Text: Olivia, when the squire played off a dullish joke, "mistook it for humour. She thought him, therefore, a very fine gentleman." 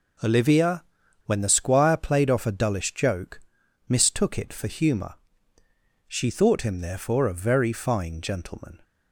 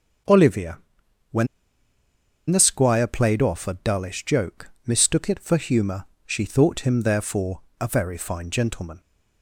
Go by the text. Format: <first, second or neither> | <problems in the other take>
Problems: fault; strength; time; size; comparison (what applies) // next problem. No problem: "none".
first | starts louder than the rest; until 2.8 s; 7 dB // pauses between "when" and "the"; at 1.4 s; 1.0 s long